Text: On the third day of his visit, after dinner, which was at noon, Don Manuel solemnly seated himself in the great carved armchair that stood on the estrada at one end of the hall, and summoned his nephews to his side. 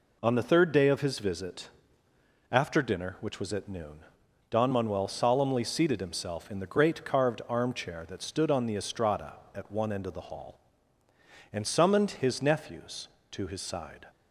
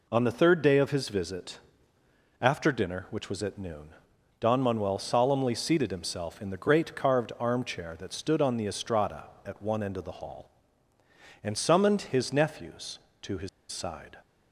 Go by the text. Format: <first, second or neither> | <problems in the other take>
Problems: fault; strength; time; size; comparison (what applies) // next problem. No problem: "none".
first | pauses between "his" and "side"; slight; at 13.4 s; 0.22 s long